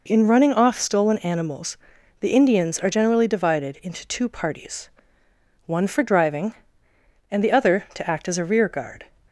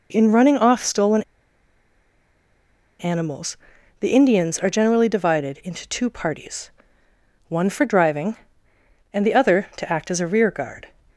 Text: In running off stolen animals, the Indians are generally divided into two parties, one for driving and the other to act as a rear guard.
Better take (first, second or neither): first